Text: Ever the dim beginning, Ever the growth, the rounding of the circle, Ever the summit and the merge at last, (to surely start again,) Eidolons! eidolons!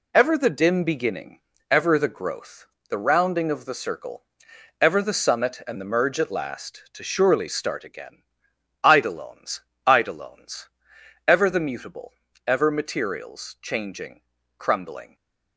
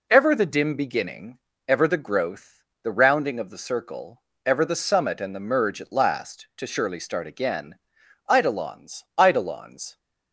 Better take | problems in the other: second | goes on to say "Ever the mutable Ever materials changing crumbling"; strong; from 11.2 s on; 3.8 s long // stays silent after the last word; slight; from 15.0 s on; 0.5 s long

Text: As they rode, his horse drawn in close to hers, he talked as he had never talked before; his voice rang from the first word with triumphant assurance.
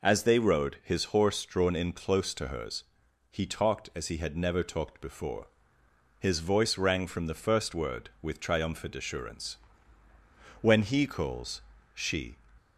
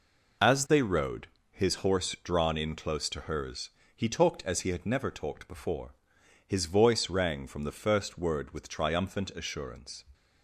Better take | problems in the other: second | goes on to say "When he calls she"; strong; from 10.6 s on; 1.7 s long

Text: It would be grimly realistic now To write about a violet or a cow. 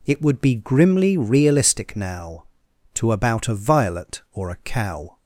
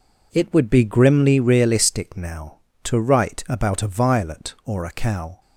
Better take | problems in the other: second | skips "write"; at 3.1 s

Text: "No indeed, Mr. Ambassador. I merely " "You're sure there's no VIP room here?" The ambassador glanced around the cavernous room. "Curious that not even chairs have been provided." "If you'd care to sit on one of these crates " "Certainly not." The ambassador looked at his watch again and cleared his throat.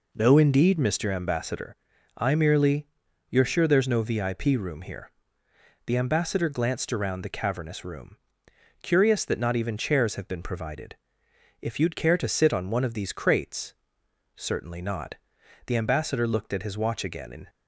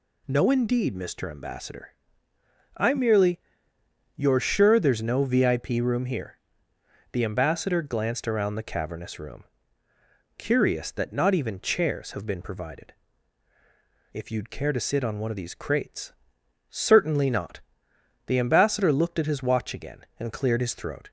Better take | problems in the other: second | stops before "cleared his throat"; at 17.4 s

